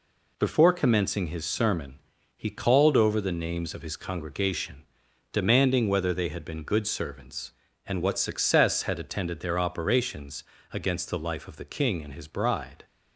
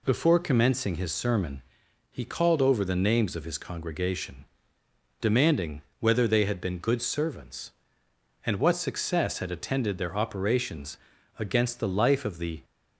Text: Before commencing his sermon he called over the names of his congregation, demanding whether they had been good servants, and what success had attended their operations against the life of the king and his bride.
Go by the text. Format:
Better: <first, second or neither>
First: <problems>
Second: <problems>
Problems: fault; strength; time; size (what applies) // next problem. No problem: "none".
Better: first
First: pauses between "sermon" and "he"; slight; at 1.9 s; 0.36 s long // pauses between "operations" and "against"; slight; at 10.4 s; 0.30 s long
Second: pauses between "sermon" and "he"; noticeable; at 1.6 s; 0.50 s long // pauses between "demanding" and "whether"; slight; at 5.8 s; 0.18 s long // pauses between "operations" and "against"; at 10.9 s; 0.40 s long // stops before "king and his bride"; at 12.6 s